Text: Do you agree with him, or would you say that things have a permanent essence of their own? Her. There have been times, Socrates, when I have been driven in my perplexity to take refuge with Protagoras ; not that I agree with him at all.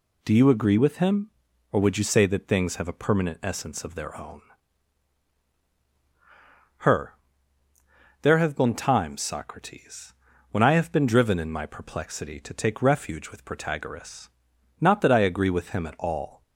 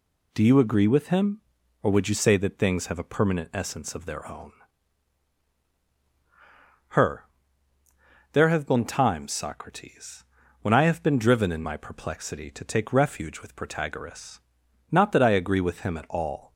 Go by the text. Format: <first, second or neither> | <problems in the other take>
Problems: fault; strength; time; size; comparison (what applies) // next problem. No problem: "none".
neither | none